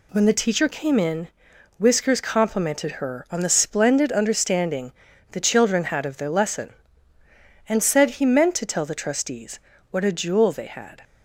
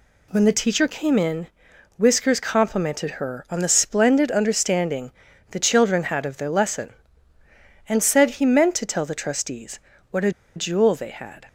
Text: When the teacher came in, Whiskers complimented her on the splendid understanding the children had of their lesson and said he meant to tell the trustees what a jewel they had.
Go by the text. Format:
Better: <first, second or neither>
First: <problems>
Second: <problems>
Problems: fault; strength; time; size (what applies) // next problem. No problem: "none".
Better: first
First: pauses between "understanding" and "the"; at 4.8 s; 0.40 s long // pauses between "trustees" and "what"; slight; at 9.5 s; 0.32 s long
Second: pauses between "understanding" and "the"; at 5.0 s; 0.40 s long // pauses between "trustees" and "what"; slight; at 9.7 s; 0.32 s long // pauses between "a" and "jewel"; slight; at 10.3 s; 0.24 s long